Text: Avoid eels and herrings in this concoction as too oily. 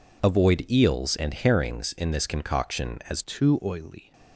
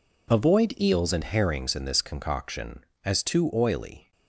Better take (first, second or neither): second